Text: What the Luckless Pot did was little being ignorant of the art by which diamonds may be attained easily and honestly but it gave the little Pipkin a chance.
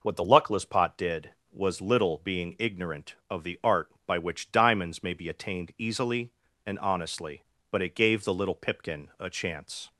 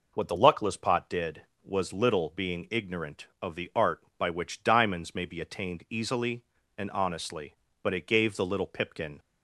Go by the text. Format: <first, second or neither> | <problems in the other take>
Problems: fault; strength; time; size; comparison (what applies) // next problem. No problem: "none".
first | stops before "a chance"; at 9.1 s